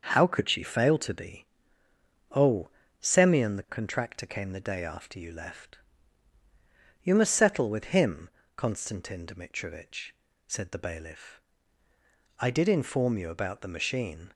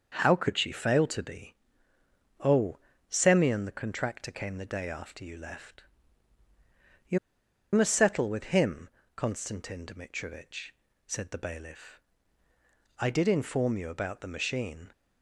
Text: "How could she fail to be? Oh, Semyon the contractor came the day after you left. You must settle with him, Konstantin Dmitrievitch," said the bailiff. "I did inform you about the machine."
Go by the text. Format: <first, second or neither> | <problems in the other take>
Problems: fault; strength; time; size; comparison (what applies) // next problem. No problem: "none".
first | starts louder than the rest; until 1.1 s; 6 dB; noticeable in the first // pauses between "You" and "must"; noticeable; at 7.1 s; 0.54 s long